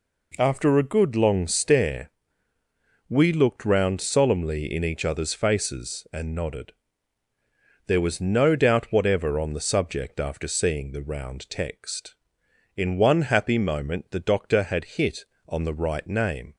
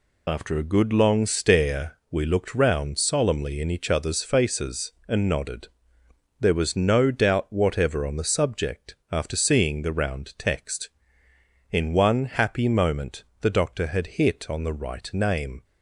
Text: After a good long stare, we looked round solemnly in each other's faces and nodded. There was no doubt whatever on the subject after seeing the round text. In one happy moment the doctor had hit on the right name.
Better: first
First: none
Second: loses the start of "After"; at 0.2 s; 45 ms // pauses between "subject" and "after"; slight; at 8.9 s; 0.16 s long // pauses between "moment" and "the"; slight; at 13.2 s; 0.18 s long

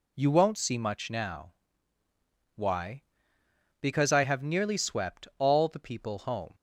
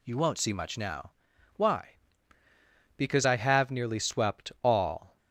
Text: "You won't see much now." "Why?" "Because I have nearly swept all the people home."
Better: first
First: none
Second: stops before "the people home"; at 5.1 s

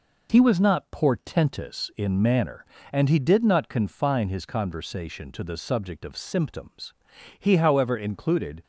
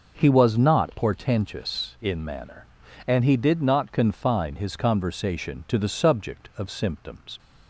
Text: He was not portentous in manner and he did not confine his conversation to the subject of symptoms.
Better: second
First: goes on to say "He however included"; noticeable; from 7.3 s on; 1.2 s long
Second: none

